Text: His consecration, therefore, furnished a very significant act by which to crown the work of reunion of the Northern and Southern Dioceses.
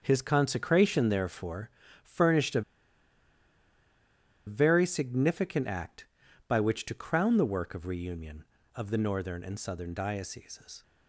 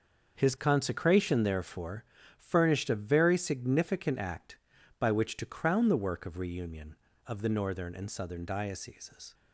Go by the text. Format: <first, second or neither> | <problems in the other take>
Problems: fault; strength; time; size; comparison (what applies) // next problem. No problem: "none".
second | starts louder than the rest; until 1.0 s; 6.5 dB; also in the second // pauses between "a" and "very"; strong; at 2.6 s; 1.8 s long